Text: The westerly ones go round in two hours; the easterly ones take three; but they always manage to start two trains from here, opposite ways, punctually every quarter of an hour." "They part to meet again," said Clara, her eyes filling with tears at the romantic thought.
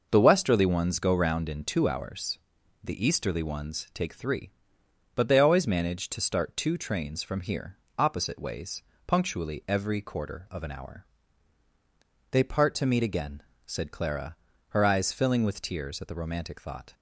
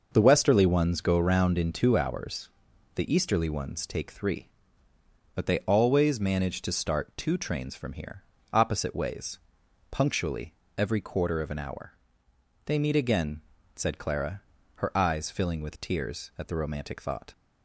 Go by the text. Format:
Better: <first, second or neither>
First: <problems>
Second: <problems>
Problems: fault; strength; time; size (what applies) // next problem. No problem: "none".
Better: first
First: none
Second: pauses between "punctually" and "every"; slight; at 10.5 s; 0.24 s long // skips "part to"; at 12.7 s